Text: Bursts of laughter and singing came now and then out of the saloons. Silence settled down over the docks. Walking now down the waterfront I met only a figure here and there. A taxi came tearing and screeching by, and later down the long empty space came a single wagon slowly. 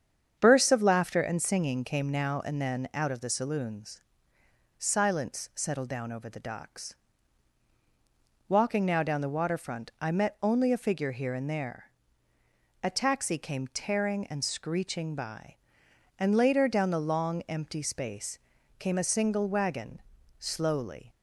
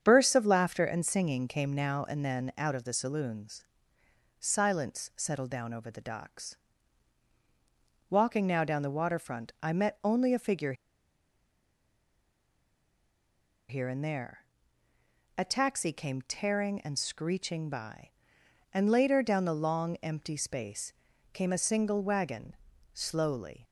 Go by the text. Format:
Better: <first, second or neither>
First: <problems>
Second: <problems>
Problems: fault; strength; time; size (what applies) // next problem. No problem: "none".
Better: first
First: starts louder than the rest; strong; until 1.4 s; 8 dB // pauses between "space" and "came"; at 18.3 s; 0.40 s long // pauses between "wagon" and "slowly"; at 19.9 s; 0.38 s long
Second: starts louder than the rest; strong; until 1.0 s; 8 dB // pauses between "figure" and "here"; strong; at 10.7 s; 2.9 s long // pauses between "space" and "came"; at 20.9 s; 0.40 s long // pauses between "wagon" and "slowly"; at 22.5 s; 0.38 s long